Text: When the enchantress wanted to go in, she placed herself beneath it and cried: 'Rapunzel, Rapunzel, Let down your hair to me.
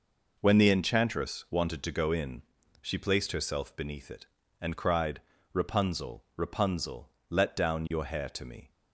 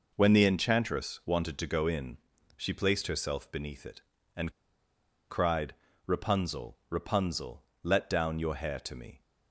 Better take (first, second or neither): first